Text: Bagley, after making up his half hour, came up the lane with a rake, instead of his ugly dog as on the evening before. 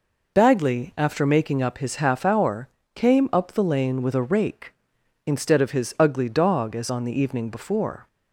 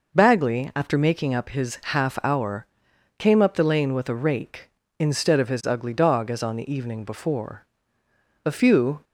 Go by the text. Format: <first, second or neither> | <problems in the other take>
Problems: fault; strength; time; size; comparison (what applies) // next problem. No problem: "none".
first | goes on to say "A few"; from 8.4 s on; 0.58 s long